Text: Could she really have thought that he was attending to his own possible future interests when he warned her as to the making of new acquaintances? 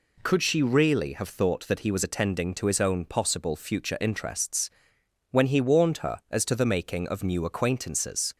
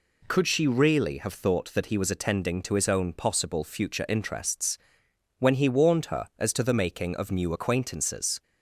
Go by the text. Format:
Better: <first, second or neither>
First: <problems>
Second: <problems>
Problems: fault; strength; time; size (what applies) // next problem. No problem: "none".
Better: neither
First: pauses between "interests" and "when"; noticeable; at 4.6 s; 0.62 s long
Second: pauses between "interests" and "when"; noticeable; at 4.7 s; 0.62 s long